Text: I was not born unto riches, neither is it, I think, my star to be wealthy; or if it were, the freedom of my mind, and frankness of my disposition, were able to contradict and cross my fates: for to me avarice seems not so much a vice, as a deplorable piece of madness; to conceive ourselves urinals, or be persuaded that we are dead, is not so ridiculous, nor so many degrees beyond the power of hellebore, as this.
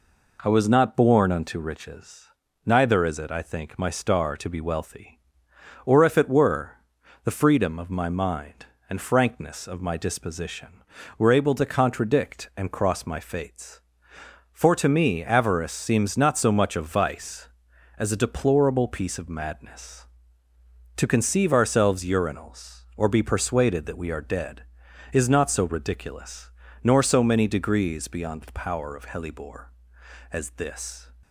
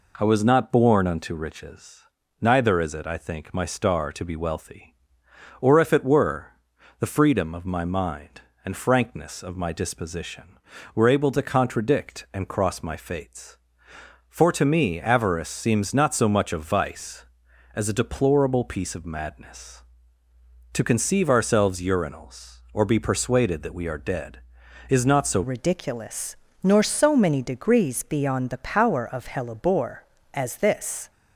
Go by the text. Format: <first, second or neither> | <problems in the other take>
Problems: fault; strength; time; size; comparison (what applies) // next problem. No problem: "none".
first | changes voice at "ridiculous"; from 25.4 s on; 5.7 s long